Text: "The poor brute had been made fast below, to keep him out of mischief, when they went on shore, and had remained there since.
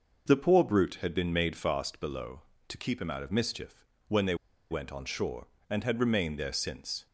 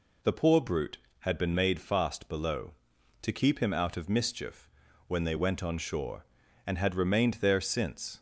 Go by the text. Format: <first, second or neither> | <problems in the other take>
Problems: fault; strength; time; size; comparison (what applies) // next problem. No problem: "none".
second | pauses between "they" and "went"; slight; at 4.3 s; 0.35 s long